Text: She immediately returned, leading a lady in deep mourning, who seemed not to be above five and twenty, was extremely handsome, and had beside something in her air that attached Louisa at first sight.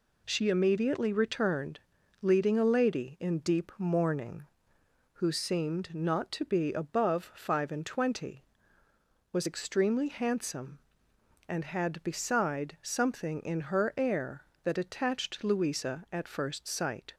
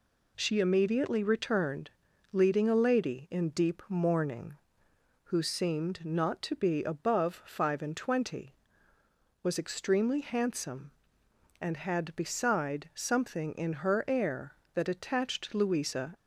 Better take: first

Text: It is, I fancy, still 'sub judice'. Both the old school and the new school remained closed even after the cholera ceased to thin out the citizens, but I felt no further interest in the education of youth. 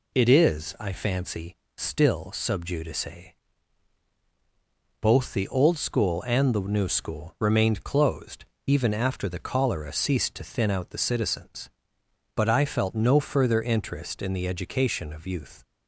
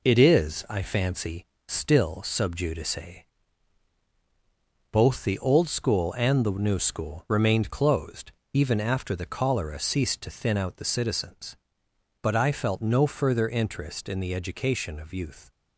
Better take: first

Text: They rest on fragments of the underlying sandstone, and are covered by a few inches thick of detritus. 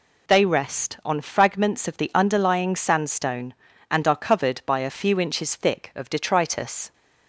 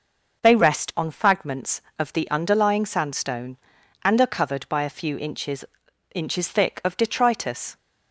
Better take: first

